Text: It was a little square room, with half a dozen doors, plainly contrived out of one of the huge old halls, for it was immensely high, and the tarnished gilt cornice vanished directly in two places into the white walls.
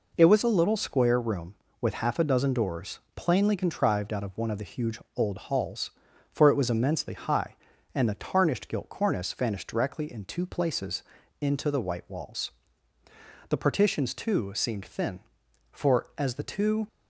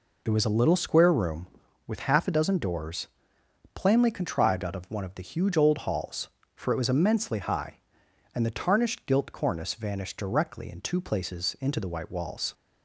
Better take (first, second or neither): second